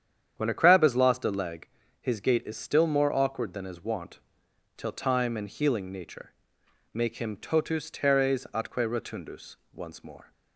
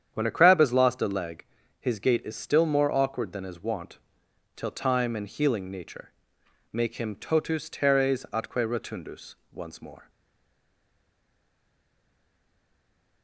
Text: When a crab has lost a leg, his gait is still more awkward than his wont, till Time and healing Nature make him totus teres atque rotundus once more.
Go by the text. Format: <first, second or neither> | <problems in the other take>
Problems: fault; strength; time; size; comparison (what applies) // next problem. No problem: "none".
first | starts louder than the rest; strong; until 1.1 s; 8.5 dB; strong in the first // pauses between "Nature" and "make"; noticeable; at 6.1 s; 0.60 s long; noticeable in the first // pauses between "rotundus" and "once"; slight; at 9.3 s; 0.18 s long; slight in the first // stays silent after the last word; strong; from 10.0 s on; 3.2 s long